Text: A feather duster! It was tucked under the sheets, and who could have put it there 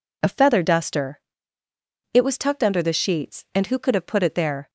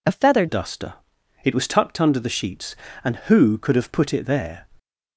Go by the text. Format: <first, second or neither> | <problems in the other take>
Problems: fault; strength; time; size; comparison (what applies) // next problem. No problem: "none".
first | changes voice at "duster"; from 0.4 s on; 4.2 s long